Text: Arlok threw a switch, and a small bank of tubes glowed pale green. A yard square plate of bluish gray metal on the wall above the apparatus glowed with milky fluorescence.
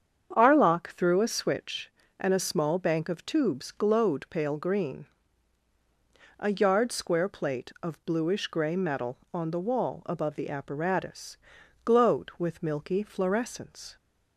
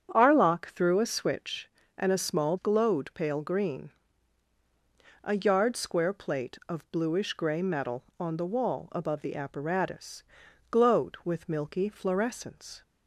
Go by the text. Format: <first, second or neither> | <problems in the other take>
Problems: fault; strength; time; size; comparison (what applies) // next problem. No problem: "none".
first | starts louder than the rest; strong; until 1.1 s; 8 dB; strong in the first // skips "bank of tubes"; at 2.5 s // pauses between "apparatus" and "glowed"; noticeable; at 10.2 s; 0.48 s long; noticeable in the first